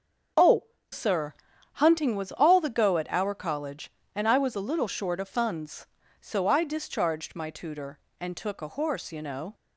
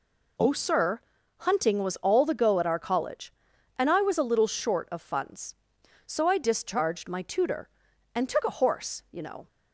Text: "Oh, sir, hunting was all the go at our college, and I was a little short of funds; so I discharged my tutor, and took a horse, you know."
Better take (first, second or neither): second